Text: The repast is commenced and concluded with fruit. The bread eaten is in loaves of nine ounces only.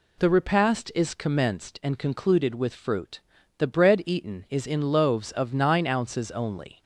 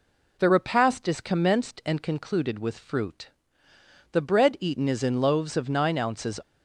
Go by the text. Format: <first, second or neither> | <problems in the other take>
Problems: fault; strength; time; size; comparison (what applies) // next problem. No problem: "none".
first | stops before "only"; at 6.4 s